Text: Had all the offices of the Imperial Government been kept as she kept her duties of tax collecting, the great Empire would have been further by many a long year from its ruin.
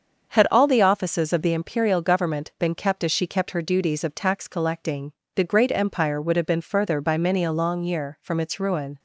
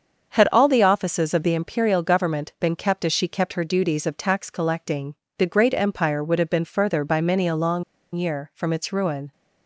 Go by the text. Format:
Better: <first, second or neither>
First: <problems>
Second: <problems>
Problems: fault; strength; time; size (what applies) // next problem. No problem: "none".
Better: first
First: starts louder than the rest; until 1.3 s; 7 dB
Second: starts louder than the rest; until 1.3 s; 7 dB // pauses between "long" and "year"; slight; at 7.8 s; 0.31 s long